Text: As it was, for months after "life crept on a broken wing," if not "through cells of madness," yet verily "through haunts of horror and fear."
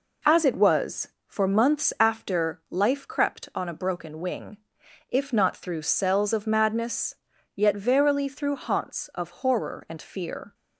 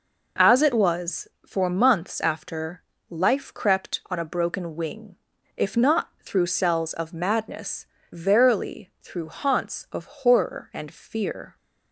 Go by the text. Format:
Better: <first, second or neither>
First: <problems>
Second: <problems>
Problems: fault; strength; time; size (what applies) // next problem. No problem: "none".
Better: first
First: none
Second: pauses between "after" and "life"; slight; at 2.8 s; 0.26 s long // skips "yet"; at 7.9 s // pauses between "of" and "horror"; slight; at 10.0 s; 0.16 s long